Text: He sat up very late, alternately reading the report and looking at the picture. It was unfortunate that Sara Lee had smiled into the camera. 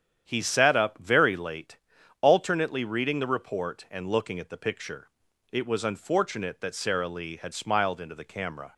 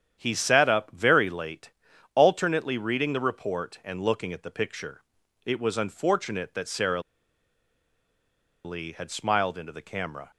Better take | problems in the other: first | starts louder than the rest; strong; until 1.2 s; 9 dB; strong in the first // pauses between "Sara" and "Lee"; strong; at 7.0 s; 1.6 s long

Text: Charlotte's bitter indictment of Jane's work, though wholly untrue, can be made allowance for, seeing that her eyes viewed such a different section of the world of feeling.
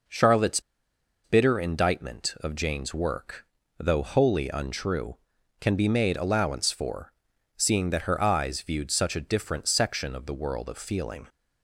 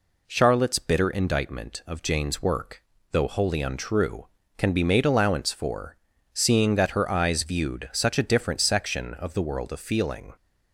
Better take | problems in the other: second | pauses between "Charlotte's" and "bitter"; noticeable; at 0.5 s; 0.64 s long

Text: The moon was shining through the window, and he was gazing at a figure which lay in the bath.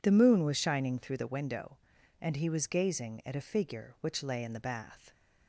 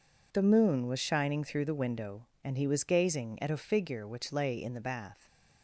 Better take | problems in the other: neither | none

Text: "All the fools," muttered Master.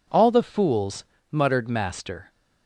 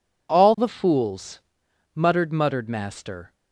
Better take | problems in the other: first | says "muttered" twice; at 2.3 s

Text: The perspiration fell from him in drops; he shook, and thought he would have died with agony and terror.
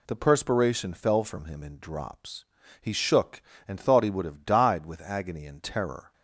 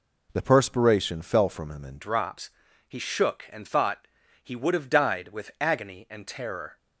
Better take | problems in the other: first | changes voice at "drops"; from 1.9 s on; 4.8 s long // pauses between "thought" and "he"; at 4.0 s; 0.38 s long

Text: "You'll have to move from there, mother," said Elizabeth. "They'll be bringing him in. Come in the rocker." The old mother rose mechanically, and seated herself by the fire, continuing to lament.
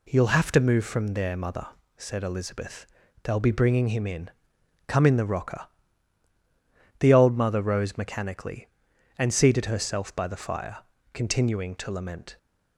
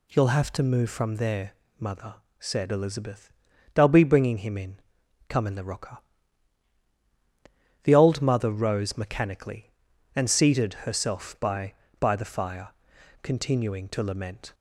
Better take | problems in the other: first | says "by" twice; at 11.9 s

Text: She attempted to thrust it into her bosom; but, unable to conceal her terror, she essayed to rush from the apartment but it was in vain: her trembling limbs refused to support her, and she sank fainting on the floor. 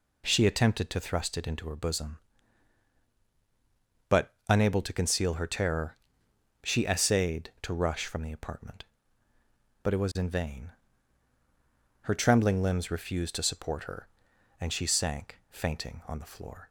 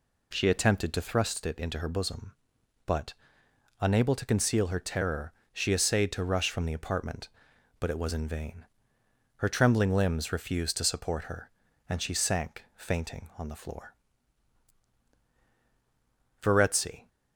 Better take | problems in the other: first | goes on to say "Verezzi"; noticeable; from 16.4 s on; 0.68 s long

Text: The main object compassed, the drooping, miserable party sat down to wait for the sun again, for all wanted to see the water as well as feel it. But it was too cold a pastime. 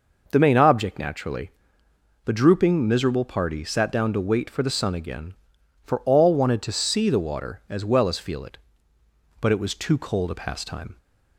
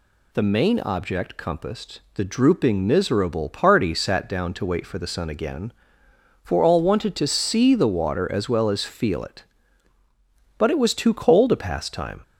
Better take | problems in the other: second | says "naturally" for "compassed"; at 0.9 s

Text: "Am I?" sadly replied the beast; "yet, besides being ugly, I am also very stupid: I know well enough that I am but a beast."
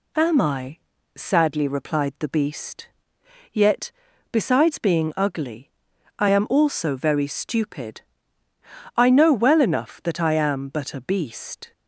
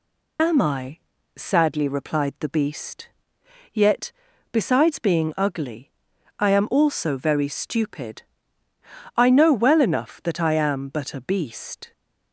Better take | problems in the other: first | loses the start of "Am"; at 0.3 s; 50 ms

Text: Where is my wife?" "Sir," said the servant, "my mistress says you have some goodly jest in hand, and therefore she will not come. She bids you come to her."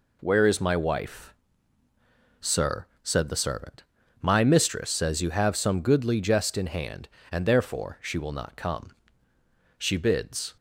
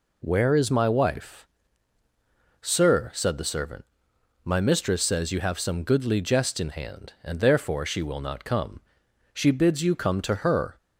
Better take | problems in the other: second | stops before "you come to her"; at 10.5 s

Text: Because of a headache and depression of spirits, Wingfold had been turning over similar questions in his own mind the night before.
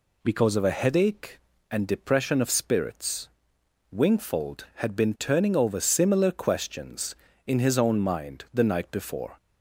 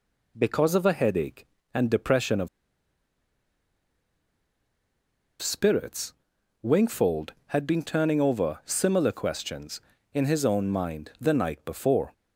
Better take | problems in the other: first | pauses between "of" and "spirits"; strong; at 2.4 s; 2.9 s long

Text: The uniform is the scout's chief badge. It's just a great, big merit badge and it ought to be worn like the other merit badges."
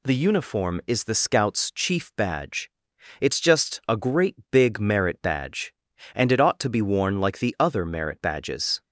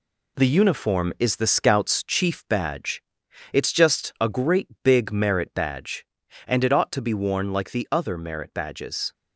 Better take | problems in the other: first | gets quieter; strong; throughout; 7 dB

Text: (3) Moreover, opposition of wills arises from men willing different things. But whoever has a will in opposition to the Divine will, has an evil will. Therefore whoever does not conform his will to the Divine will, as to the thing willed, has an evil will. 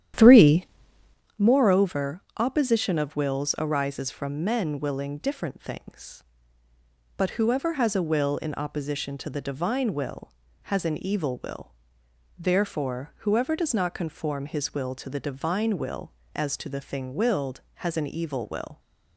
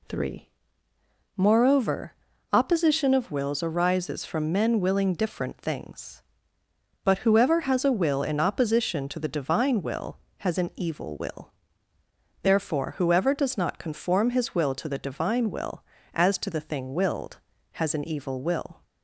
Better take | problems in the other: second | starts louder than the rest; strong; until 1.4 s; 10.5 dB

